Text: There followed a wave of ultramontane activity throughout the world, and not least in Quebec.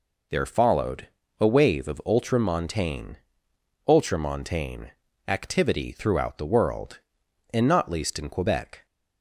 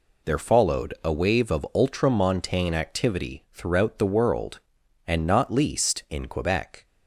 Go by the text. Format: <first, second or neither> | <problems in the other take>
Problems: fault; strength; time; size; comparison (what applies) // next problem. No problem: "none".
second | pauses between "followed" and "a"; slight; at 1.0 s; 0.32 s long // says "ultramontane" twice; at 3.8 s